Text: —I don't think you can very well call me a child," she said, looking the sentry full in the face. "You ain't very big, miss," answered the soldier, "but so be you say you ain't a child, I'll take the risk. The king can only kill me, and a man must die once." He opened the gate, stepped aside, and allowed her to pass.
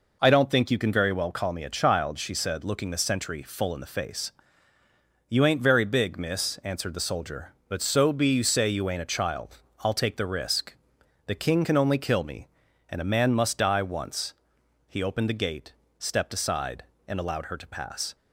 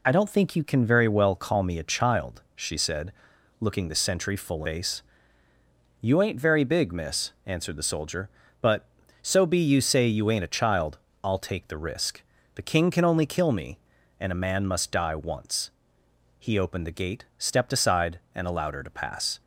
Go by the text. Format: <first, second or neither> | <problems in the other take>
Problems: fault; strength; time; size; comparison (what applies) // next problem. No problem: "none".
first | skips "in the"; at 4.6 s